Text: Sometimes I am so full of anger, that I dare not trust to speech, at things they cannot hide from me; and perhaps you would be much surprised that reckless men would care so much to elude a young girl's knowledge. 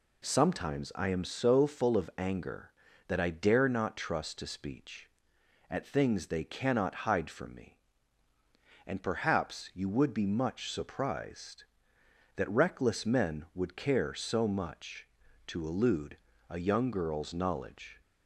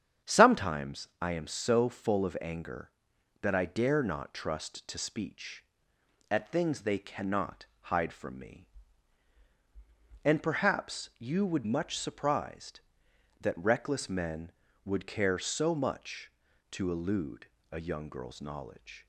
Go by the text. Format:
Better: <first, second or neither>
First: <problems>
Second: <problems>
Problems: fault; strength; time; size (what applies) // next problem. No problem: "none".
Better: first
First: pauses between "elude" and "a"; slight; at 16.1 s; 0.30 s long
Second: starts louder than the rest; strong; until 1.3 s; 8.5 dB // pauses between "cannot" and "hide"; slight; at 7.6 s; 0.16 s long // skips "be"; at 11.6 s // pauses between "elude" and "a"; slight; at 17.4 s; 0.22 s long